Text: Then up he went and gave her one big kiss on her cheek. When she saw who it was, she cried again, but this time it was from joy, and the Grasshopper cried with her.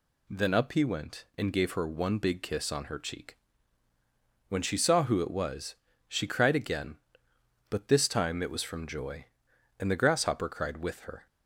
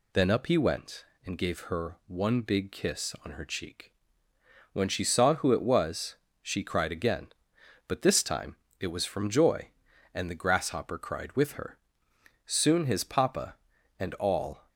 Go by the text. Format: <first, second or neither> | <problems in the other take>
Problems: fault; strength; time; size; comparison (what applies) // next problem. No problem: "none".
first | pauses between "time" and "it"; slight; at 8.5 s; 0.24 s long // goes on to say "Soon his papa and all"; strong; from 12.4 s on; 2.2 s long